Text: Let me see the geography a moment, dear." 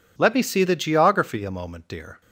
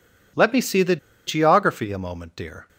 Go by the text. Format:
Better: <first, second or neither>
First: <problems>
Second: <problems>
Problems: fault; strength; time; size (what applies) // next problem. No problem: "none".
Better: first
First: none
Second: pauses between "the" and "geography"; slight; at 0.9 s; 0.30 s long